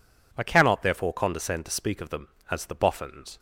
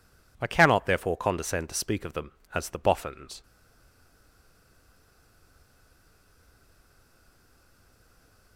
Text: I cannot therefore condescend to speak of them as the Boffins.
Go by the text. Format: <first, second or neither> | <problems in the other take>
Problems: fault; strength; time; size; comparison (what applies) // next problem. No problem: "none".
first | stays silent after the last word; strong; from 3.4 s on; 5.1 s long